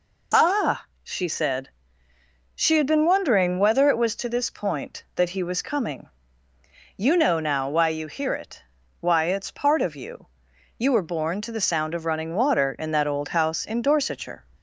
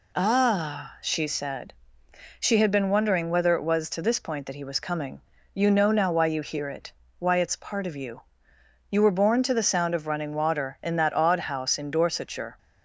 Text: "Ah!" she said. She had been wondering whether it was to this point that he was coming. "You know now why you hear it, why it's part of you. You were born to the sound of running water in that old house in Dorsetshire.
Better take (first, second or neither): first